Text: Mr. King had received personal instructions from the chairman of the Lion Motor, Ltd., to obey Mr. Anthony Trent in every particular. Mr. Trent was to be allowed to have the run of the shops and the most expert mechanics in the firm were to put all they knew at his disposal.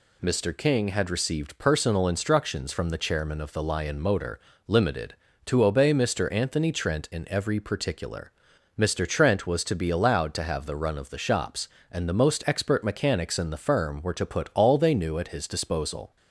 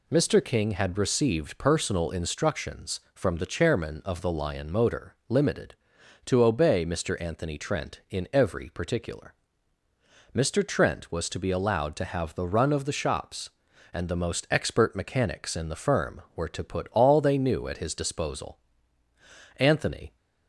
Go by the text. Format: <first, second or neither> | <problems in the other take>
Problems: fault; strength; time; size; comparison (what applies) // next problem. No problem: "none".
first | goes on to say "Anthony"; from 19.5 s on; 0.58 s long